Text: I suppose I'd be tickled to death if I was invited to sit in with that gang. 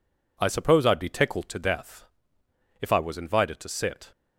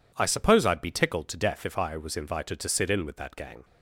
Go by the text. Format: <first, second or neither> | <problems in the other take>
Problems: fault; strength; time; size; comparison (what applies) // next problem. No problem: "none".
second | pauses between "death" and "if"; noticeable; at 2.0 s; 0.74 s long // stops before "in with that gang"; at 4.1 s